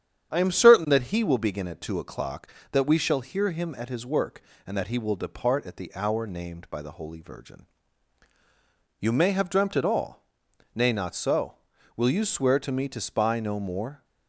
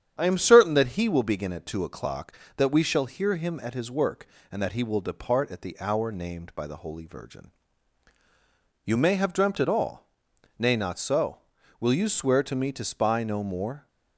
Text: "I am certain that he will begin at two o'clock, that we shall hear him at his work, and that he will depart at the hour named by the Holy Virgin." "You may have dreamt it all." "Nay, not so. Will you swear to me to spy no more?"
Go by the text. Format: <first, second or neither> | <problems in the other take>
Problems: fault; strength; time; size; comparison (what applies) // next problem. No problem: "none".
neither | starts louder than the rest; strong; the same in both